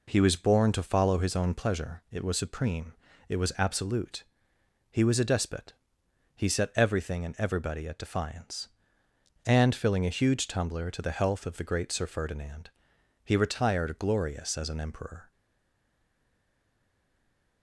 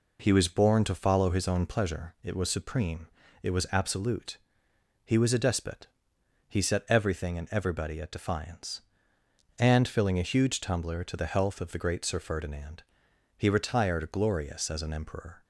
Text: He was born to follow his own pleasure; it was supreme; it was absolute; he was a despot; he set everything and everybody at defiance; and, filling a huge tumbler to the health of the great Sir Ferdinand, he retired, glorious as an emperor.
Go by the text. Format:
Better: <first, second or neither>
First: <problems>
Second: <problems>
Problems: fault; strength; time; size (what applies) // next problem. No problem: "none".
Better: second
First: stays silent after the last word; from 15.3 s on; 2.3 s long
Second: none